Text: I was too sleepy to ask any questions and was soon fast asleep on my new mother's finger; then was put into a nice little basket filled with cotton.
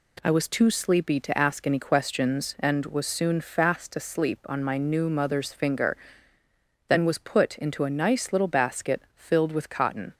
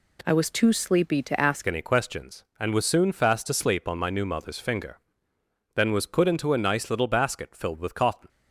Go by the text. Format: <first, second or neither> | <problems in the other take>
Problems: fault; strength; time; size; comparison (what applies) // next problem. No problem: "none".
first | changes voice at "any"; from 1.6 s on; 6.6 s long